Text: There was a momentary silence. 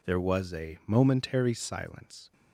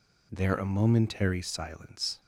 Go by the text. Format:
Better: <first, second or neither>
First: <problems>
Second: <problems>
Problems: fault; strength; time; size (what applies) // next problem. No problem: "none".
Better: first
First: none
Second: skips "was"; at 0.5 s